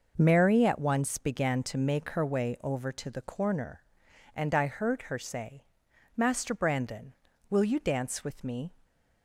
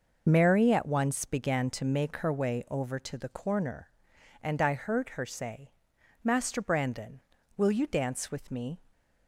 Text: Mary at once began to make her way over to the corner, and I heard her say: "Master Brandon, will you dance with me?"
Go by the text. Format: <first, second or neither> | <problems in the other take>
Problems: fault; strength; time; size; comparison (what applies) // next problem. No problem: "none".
first | loses the start of "Mary"; at 0.2 s; 45 ms